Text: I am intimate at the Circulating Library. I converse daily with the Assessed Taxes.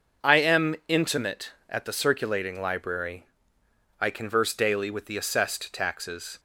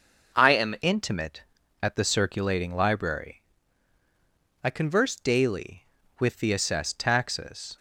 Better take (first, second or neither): first